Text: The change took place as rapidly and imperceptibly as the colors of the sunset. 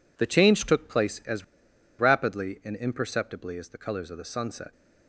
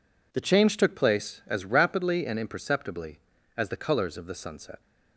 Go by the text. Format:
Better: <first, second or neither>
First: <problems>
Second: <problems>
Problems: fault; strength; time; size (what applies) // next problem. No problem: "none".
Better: second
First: pauses between "as" and "rapidly"; noticeable; at 1.4 s; 0.54 s long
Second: none